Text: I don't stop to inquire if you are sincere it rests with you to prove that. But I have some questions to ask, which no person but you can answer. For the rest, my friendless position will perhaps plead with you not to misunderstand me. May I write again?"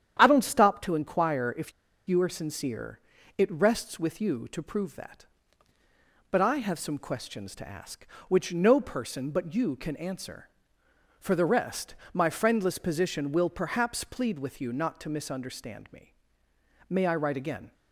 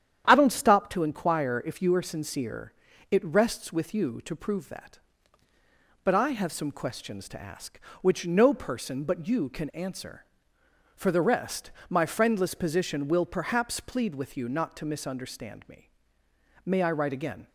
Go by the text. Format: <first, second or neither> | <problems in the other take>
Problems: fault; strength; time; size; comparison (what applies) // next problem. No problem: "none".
second | starts louder than the rest; strong; until 1.2 s; 9.5 dB; strong in the second // pauses between "if" and "you"; slight; at 1.7 s; 0.35 s long // pauses between "sincere" and "it"; at 2.9 s; 0.40 s long; also in the second